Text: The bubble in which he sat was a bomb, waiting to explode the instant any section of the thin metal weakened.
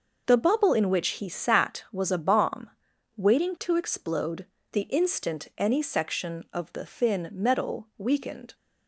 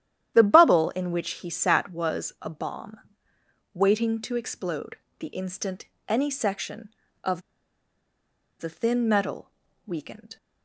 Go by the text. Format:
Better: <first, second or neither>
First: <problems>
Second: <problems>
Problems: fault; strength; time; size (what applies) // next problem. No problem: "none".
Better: first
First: pauses between "explode" and "the"; slight; at 4.4 s; 0.28 s long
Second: starts louder than the rest; strong; until 1.4 s; 11 dB // pauses between "explode" and "the"; slight; at 4.9 s; 0.22 s long // pauses between "instant" and "any"; slight; at 5.8 s; 0.20 s long // pauses between "of" and "the"; at 7.4 s; 1.1 s long // pauses between "metal" and "weakened"; slight; at 9.5 s; 0.36 s long